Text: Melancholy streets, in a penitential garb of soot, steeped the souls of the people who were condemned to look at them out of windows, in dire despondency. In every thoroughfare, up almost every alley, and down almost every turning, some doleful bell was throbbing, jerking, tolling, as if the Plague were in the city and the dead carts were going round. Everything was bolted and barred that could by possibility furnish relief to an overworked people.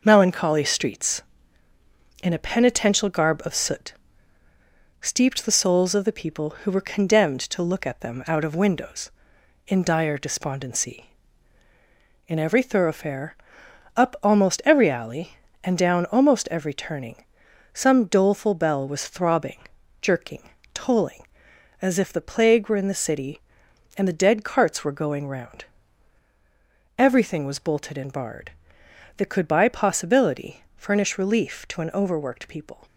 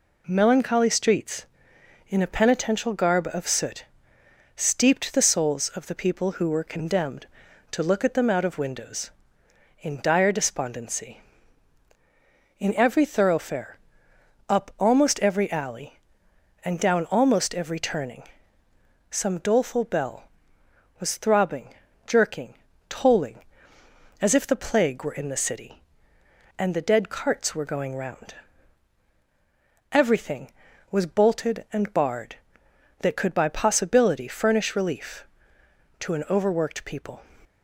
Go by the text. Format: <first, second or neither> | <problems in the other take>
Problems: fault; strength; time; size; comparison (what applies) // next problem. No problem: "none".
second | gets quieter; noticeable; throughout; 5.5 dB